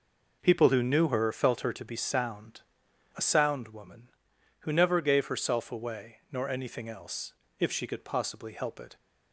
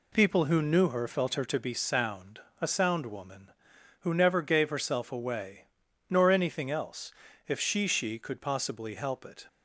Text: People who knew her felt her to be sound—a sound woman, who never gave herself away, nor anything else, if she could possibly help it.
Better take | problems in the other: first | says "she" twice; at 7.8 s

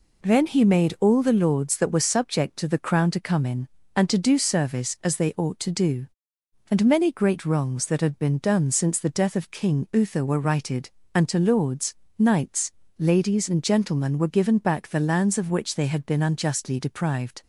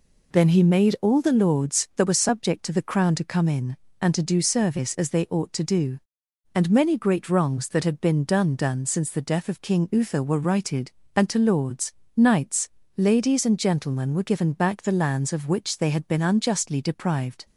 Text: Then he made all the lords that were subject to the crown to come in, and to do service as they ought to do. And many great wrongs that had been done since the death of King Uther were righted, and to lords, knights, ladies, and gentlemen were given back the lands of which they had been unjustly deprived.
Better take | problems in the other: first | says "done" twice; at 8.5 s

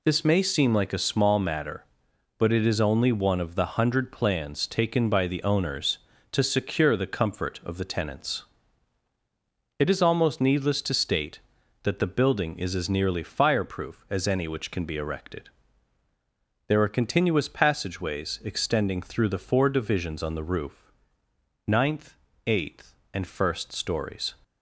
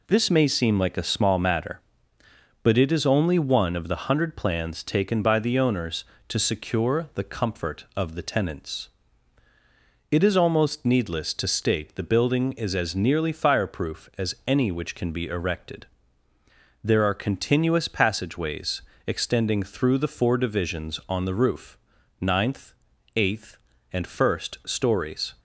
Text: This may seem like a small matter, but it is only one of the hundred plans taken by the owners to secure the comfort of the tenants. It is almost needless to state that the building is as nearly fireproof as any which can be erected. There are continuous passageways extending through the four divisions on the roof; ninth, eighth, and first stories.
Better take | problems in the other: first | skips "that"; at 11.9 s // pauses between "passageways" and "extending"; slight; at 18.8 s; 0.24 s long

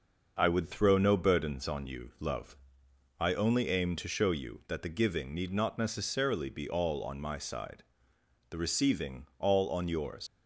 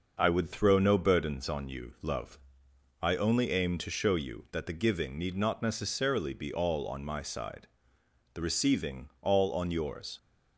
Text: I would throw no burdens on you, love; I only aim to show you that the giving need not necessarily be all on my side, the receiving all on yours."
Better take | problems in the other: second | leaves "yours" unfinished; at 10.2 s; 75 ms

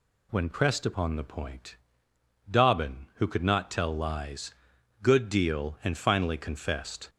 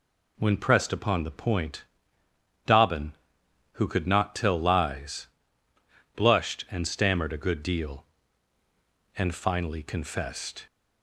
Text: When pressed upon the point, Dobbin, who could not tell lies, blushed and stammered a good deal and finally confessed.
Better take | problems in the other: second | skips "blushed and stammered a"; at 4.7 s

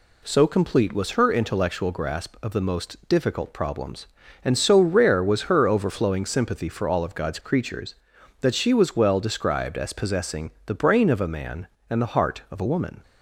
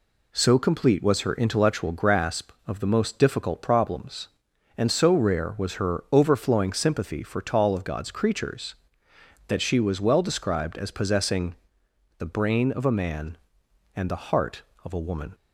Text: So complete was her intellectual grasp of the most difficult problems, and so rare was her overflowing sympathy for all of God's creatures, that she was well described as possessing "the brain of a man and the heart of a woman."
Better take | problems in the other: first | says "tall" for "all"; at 7.4 s // pauses between "possessing" and "the"; noticeable; at 11.5 s; 0.62 s long; slight in the first

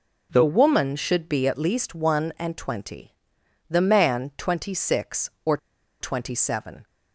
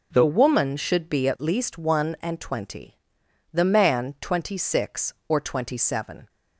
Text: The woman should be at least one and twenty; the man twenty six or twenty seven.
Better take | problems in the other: second | pauses between "or" and "twenty"; at 5.5 s; 0.43 s long

